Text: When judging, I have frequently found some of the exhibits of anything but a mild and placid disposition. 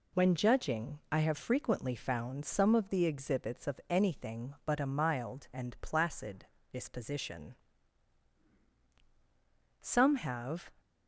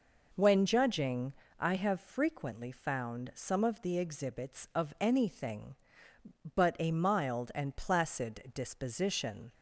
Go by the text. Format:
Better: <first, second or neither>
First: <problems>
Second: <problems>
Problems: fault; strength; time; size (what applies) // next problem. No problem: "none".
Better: second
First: pauses between "placid" and "disposition"; slight; at 6.4 s; 0.26 s long // goes on to say "Some have"; noticeable; from 9.8 s on; 0.92 s long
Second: none